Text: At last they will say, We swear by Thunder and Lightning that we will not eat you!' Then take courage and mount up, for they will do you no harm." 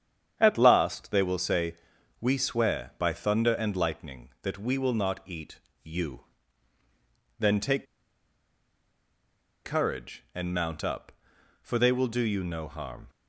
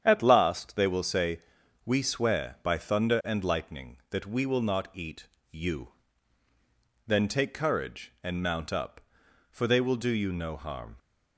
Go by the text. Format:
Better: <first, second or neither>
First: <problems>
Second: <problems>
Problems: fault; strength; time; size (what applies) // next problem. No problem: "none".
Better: second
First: starts louder than the rest; strong; until 1.4 s; 8.5 dB // pauses between "eat" and "you"; slight; at 5.5 s; 0.26 s long // pauses between "take" and "courage"; strong; at 7.8 s; 1.7 s long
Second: starts louder than the rest; strong; until 1.0 s; 8.5 dB // pauses between "eat" and "you"; slight; at 5.2 s; 0.26 s long